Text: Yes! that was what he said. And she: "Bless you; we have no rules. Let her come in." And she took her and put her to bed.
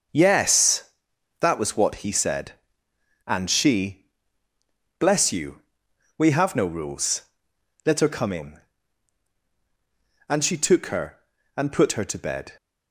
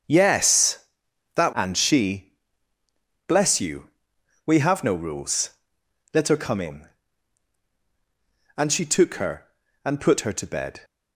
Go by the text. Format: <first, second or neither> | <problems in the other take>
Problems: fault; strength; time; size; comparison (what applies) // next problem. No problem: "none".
first | starts louder than the rest; until 1.5 s; 6.5 dB; noticeable in the first // skips "was what he said"; at 1.5 s